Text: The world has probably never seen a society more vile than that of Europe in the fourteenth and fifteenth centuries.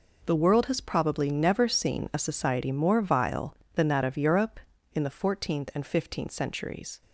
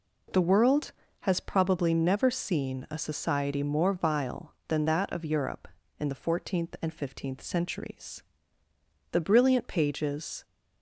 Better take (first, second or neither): first